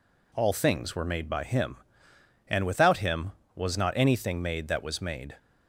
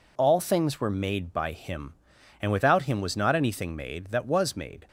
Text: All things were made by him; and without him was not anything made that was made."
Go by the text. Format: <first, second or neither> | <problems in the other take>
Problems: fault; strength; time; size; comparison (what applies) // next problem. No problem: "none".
neither | none